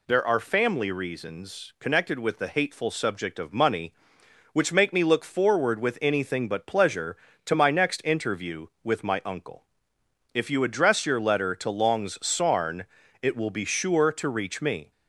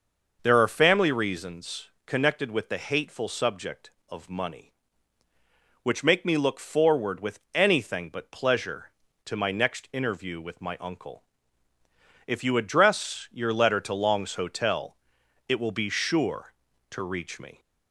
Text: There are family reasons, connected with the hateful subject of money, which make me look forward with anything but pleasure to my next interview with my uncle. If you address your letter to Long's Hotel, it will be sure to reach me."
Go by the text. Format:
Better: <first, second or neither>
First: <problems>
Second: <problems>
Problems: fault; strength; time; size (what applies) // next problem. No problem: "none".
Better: second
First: says "Sarn" for "Hotel"; at 12.2 s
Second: none